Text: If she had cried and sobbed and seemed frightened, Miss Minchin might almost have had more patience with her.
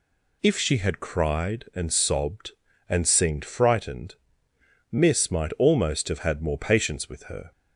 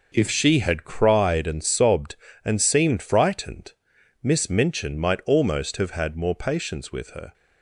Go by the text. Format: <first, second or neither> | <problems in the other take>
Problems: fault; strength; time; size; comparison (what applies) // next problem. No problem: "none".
second | skips "Minchin"; at 5.2 s